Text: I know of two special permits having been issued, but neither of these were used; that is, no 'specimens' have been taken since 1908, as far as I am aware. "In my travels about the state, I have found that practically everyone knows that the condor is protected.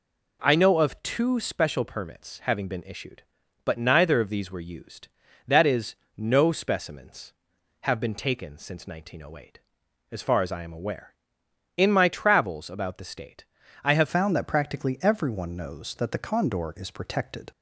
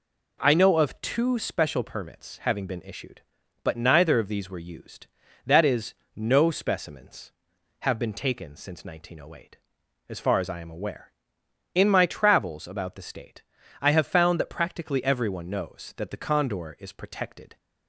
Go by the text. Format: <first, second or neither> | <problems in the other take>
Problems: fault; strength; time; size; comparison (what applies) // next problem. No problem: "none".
second | changes voice at "found"; from 14.0 s on; 3.4 s long